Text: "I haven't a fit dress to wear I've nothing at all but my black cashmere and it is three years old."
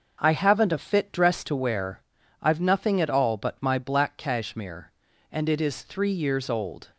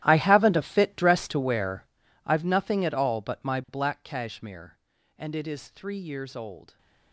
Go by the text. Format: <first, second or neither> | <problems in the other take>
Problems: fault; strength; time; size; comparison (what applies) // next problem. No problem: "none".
first | gets quieter; strong; throughout; 18 dB // starts louder than the rest; strong; until 1.0 s; 13 dB; noticeable in the first // pauses between "wear" and "I've"; at 1.8 s; 0.40 s long; also in the first